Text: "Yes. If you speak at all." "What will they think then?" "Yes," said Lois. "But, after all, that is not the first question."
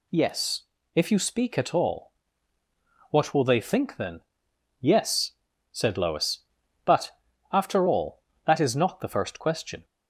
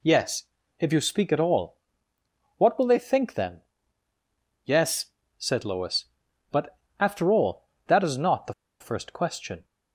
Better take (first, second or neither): first